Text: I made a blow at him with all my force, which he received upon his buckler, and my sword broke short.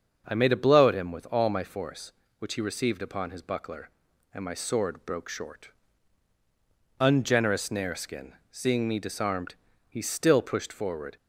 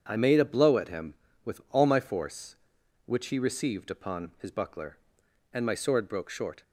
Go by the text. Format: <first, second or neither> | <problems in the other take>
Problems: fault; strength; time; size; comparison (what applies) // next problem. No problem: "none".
second | starts louder than the rest; until 1.2 s; 6.5 dB // goes on to say "Ungenerous Nareskin seeing me disarmed he still pushed forward"; strong; from 6.9 s on; 4.1 s long